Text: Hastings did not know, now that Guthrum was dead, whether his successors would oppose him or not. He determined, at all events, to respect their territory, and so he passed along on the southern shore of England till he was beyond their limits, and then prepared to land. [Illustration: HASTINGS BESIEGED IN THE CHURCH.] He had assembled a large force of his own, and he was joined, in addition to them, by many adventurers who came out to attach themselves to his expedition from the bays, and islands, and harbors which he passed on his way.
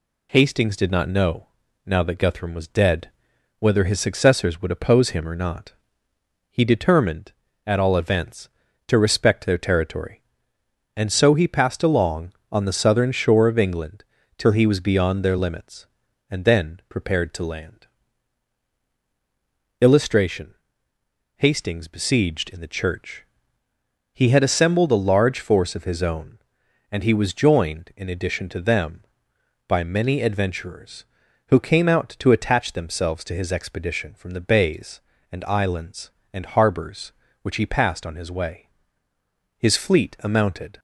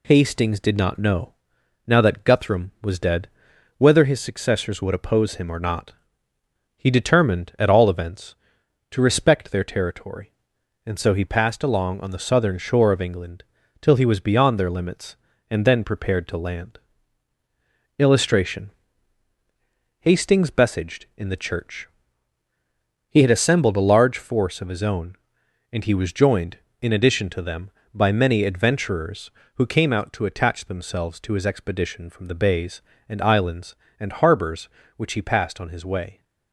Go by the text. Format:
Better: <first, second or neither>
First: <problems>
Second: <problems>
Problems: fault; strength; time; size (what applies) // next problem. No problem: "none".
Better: second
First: pauses between "England" and "till"; slight; at 14.0 s; 0.34 s long // goes on to say "His fleet amounted"; noticeable; from 39.5 s on; 1.2 s long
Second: pauses between "England" and "till"; slight; at 13.4 s; 0.36 s long